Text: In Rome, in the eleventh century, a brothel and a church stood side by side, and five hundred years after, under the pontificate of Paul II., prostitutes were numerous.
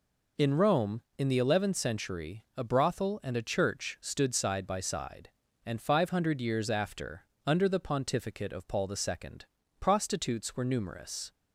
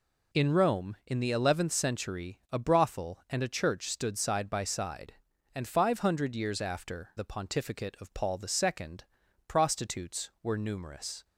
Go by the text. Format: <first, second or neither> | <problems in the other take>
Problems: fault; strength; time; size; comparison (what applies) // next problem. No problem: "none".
first | skips "under"; at 7.1 s